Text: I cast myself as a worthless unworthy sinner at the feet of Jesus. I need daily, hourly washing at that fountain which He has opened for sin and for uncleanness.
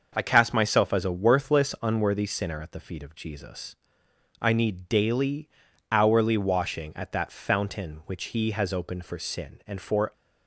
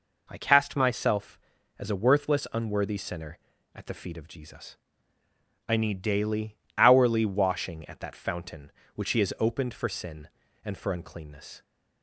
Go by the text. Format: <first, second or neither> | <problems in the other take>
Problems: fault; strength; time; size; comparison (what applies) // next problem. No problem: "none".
second | starts louder than the rest; noticeable; until 1.1 s; 6 dB // stops before "uncleanness"; at 10.1 s